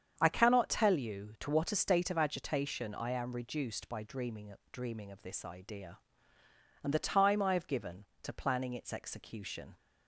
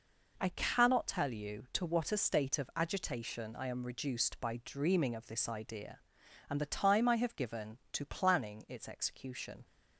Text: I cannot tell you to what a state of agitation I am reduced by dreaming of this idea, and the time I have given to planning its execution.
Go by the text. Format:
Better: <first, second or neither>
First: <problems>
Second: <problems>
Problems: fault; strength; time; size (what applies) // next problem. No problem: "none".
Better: second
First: starts louder than the rest; strong; until 1.1 s; 8 dB // says "dreaming" twice; at 4.7 s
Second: none